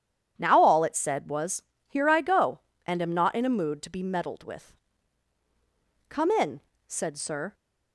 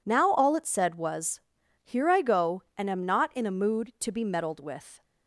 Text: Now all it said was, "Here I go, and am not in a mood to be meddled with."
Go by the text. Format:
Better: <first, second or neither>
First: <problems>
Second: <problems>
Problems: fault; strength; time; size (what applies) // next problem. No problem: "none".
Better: second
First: goes on to say "Come in said Sir"; from 6.0 s on; 1.4 s long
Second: none